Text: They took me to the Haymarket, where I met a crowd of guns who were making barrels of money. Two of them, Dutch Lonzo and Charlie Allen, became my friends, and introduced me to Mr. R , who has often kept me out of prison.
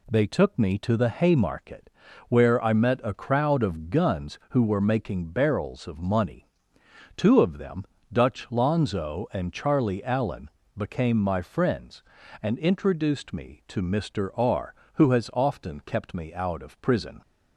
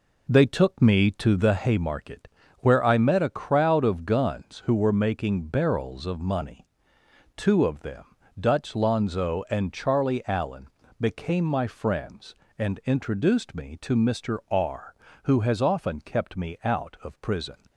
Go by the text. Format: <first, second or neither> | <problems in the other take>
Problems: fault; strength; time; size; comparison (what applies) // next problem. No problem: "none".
first | starts louder than the rest; until 1.5 s; 4 dB